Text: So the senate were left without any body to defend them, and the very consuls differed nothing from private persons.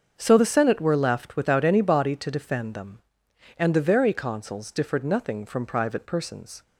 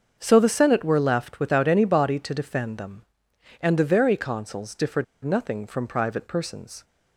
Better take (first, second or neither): first